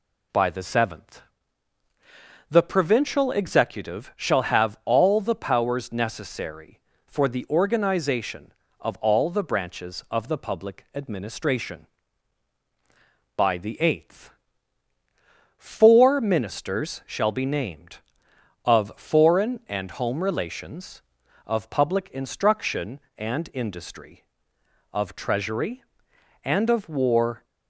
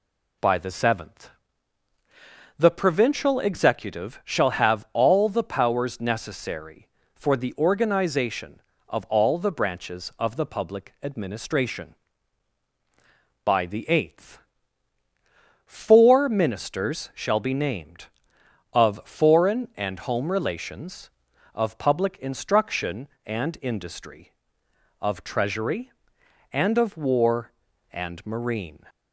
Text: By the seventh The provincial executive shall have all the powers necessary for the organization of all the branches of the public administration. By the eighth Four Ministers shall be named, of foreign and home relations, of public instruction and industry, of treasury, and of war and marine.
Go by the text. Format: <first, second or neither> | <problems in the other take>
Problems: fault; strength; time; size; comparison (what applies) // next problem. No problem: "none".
second | pauses between "seventh" and "The"; strong; at 1.2 s; 1.2 s long; strong in the second // pauses between "eighth" and "Four"; strong; at 14.3 s; 1.2 s long; strong in the second // stops before "and marine"; at 27.4 s